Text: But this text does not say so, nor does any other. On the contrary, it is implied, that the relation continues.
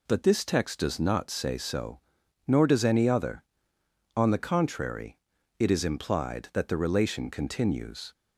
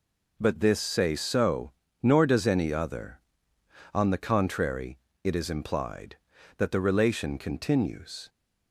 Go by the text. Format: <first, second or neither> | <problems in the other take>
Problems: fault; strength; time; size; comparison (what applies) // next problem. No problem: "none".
first | skips "text does not"; at 0.7 s